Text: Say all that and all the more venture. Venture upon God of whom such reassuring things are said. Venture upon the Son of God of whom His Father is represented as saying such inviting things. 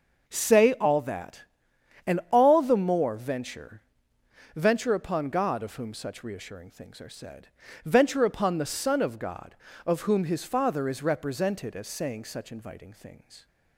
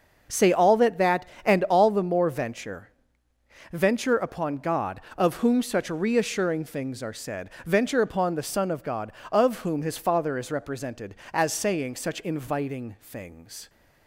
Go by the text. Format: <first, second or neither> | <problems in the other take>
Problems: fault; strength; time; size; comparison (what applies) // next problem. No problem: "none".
first | starts louder than the rest; noticeable; until 1.4 s; 6 dB; noticeable in the first // says "that" twice; at 0.9 s